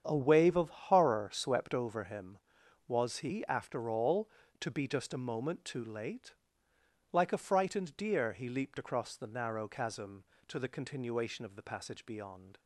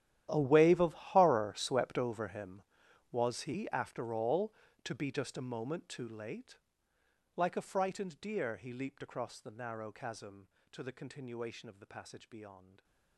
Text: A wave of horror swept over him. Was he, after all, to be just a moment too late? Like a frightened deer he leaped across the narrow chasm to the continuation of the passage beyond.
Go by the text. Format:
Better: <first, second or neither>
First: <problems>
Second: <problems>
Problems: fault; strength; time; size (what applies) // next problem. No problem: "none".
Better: first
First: starts louder than the rest; strong; until 1.0 s; 8 dB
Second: gets quieter; strong; throughout; 19 dB // starts louder than the rest; strong; until 1.3 s; 11.5 dB